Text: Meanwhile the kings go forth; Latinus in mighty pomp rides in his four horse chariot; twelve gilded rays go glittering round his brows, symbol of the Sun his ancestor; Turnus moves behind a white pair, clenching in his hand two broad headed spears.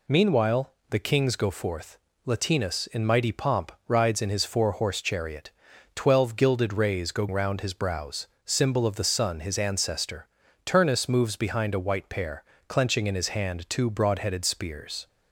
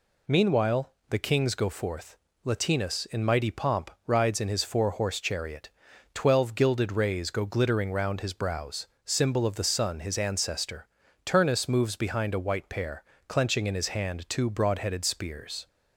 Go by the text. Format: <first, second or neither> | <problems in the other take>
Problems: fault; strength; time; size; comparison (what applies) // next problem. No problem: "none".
second | pauses between "Meanwhile" and "the"; slight; at 0.7 s; 0.20 s long; slight in the second // pauses between "pomp" and "rides"; slight; at 3.7 s; 0.16 s long; slight in the second // skips "glittering"; at 7.2 s